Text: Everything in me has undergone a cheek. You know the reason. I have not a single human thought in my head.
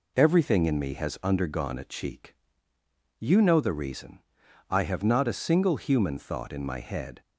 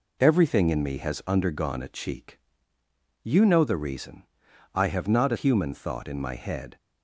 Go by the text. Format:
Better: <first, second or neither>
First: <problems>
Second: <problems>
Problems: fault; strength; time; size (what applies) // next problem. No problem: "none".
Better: first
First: none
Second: skips "single"; at 5.3 s